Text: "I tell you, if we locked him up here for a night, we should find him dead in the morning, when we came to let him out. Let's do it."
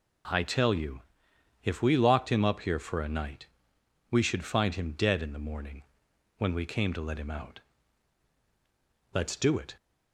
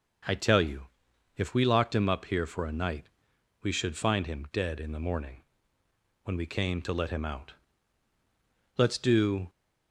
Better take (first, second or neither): first